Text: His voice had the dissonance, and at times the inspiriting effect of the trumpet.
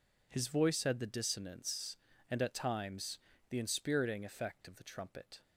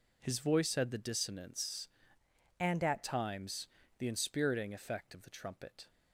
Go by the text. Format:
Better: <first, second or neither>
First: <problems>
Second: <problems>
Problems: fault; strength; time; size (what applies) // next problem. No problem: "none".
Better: first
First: pauses between "times" and "the"; slight; at 3.1 s; 0.32 s long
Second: changes voice from "and" to "at"; from 2.5 to 3.0 s; 0.5 s long // pauses between "times" and "the"; slight; at 3.6 s; 0.32 s long